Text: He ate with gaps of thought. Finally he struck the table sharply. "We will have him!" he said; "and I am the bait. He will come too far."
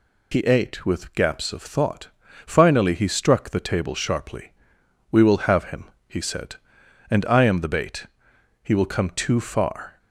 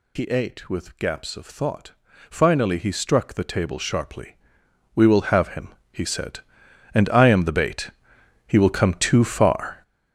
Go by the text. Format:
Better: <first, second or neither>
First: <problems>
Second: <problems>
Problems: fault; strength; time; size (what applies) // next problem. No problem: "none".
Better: first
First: none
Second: gets louder; strong; throughout; 10 dB